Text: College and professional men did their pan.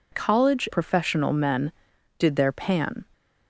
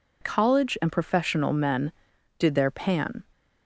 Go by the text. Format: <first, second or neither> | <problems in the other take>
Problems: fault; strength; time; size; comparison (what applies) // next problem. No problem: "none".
second | skips "and"; at 0.7 s